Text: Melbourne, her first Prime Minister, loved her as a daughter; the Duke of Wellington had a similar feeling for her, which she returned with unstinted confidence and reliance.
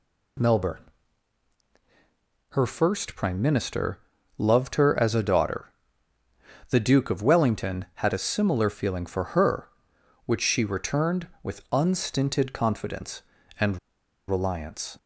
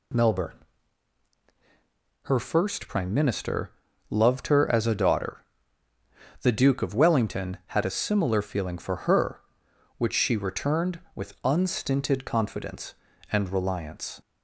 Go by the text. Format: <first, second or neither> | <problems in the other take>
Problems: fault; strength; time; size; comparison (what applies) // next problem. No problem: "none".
second | pauses between "and" and "reliance"; noticeable; at 13.7 s; 0.50 s long